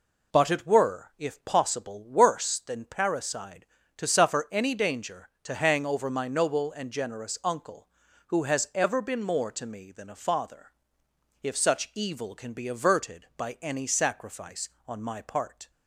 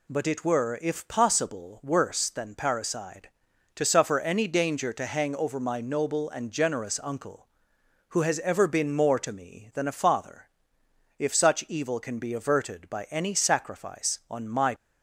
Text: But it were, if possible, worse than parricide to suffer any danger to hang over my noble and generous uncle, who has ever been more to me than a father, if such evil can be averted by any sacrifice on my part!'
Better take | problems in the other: first | stops before "part"; at 14.7 s

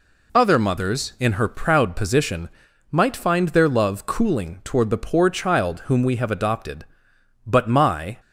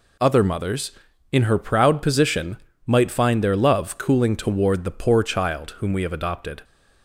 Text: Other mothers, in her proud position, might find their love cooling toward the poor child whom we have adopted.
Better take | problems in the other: second | goes on to say "But my"; noticeable; from 7.4 s on; 0.74 s long

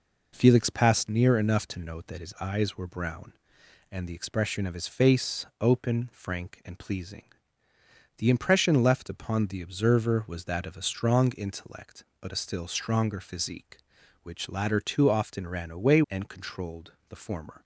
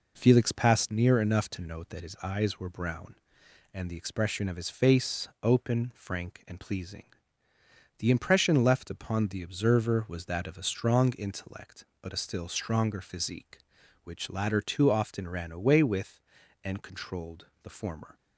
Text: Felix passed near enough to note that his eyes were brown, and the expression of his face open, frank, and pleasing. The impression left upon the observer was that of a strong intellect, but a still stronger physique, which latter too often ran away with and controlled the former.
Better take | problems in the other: second | skips "with"; at 16.0 s // pauses between "controlled" and "the"; slight; at 16.9 s; 0.16 s long; slight in the second

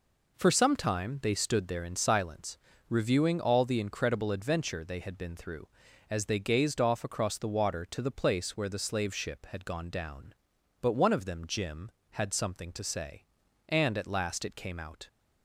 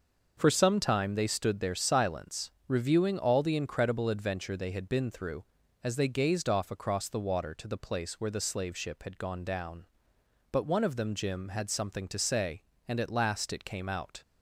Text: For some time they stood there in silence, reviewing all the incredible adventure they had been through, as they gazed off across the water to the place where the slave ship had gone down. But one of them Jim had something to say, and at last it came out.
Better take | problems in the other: first | starts louder than the rest; until 1.3 s; 6 dB // skips "in"; at 1.7 s

